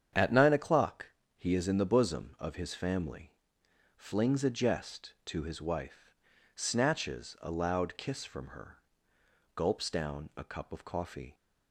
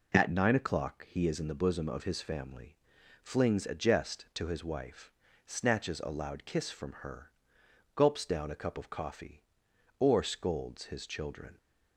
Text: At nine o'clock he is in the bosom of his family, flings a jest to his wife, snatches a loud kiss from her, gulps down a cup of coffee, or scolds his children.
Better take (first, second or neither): second